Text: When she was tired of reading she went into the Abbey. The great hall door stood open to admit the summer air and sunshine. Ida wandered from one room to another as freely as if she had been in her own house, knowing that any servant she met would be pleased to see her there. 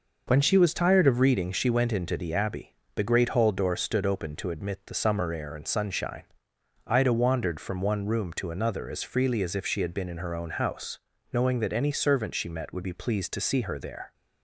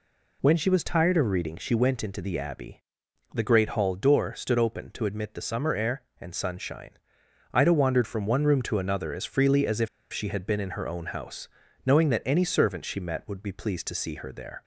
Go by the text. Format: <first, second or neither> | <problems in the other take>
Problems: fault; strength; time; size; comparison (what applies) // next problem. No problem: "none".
first | pauses between "if" and "she"; slight; at 9.8 s; 0.24 s long